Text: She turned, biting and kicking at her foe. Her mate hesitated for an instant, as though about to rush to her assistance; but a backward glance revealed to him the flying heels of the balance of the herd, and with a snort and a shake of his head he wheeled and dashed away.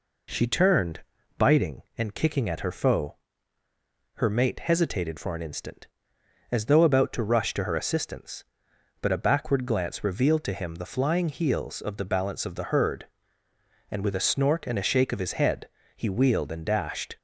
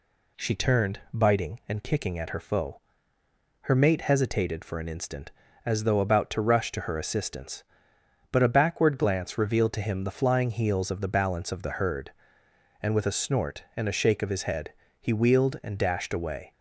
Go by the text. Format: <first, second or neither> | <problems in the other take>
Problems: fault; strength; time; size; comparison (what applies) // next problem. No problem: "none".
second | pauses between "head" and "he"; slight; at 15.6 s; 0.28 s long; slight in the second // stops before "away"; at 17.1 s